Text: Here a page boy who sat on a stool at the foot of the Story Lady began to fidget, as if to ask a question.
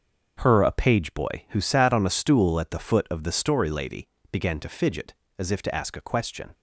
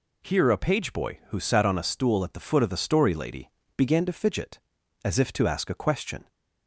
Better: second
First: starts louder than the rest; until 1.4 s; 6.5 dB // says "Her" for "Here"; at 0.4 s // pauses between "Lady" and "began"; slight; at 4.0 s; 0.24 s long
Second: pauses between "Lady" and "began"; slight; at 3.4 s; 0.26 s long

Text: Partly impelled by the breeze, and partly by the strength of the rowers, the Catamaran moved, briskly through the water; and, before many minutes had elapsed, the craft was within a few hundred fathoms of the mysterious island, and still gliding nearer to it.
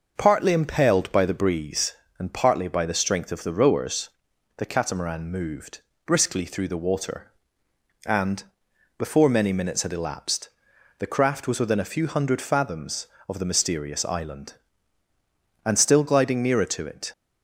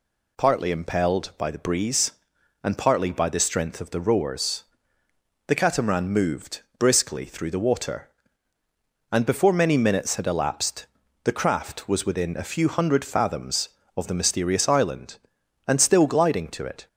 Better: first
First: none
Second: skips "nearer"; at 16.4 s

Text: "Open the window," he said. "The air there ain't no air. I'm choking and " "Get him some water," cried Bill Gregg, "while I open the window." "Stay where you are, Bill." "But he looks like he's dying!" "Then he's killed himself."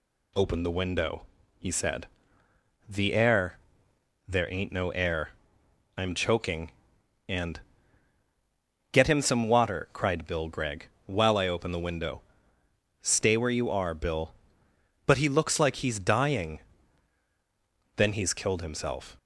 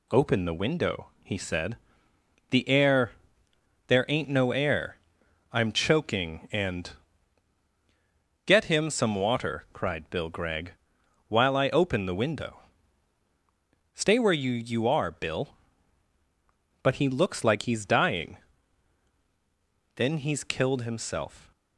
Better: first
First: pauses between "air" and "there"; noticeable; at 3.5 s; 0.70 s long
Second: pauses between "air" and "there"; noticeable; at 3.1 s; 0.76 s long // says "you" twice; at 14.5 s

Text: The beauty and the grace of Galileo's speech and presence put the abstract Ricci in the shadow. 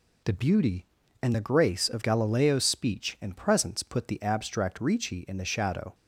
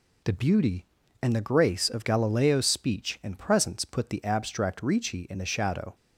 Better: neither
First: none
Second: none

